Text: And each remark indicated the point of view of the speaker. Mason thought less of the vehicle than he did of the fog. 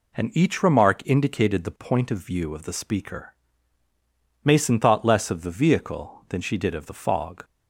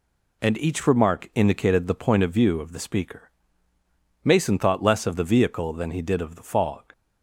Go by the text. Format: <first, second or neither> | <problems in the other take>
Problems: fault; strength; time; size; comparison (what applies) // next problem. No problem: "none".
second | says "she" for "he"; at 6.4 s